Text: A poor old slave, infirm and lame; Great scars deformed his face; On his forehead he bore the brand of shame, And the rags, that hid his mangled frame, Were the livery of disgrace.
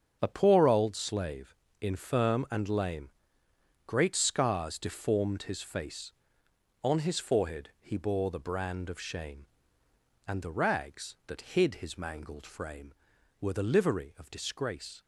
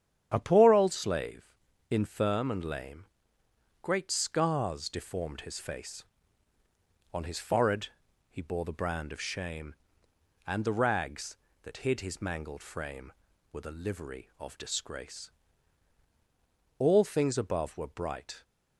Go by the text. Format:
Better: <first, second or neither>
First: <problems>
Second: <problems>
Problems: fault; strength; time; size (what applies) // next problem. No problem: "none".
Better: first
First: starts louder than the rest; strong; until 1.2 s; 7.5 dB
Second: starts louder than the rest; strong; until 1.3 s; 9.5 dB // pauses between "forehead" and "he"; at 7.8 s; 0.42 s long // goes on to say "All things above were bright"; from 16.7 s on; 1.6 s long